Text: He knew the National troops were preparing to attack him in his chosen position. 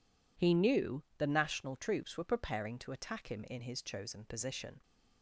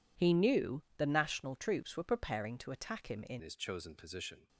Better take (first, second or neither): first